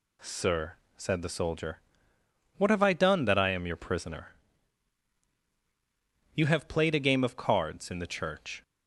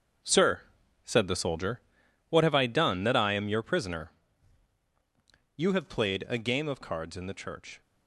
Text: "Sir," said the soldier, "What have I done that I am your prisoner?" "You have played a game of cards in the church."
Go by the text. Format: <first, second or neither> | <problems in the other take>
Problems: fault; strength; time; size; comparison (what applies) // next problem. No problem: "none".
first | gets quieter; strong; throughout; 12 dB